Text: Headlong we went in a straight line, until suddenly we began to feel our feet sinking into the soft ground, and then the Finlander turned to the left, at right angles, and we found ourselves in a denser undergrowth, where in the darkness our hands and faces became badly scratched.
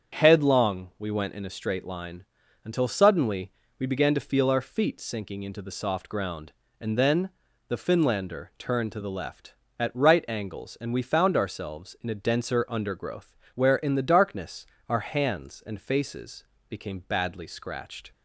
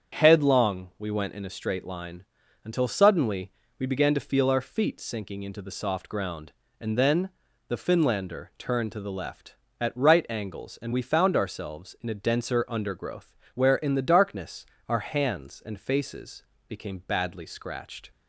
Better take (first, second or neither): neither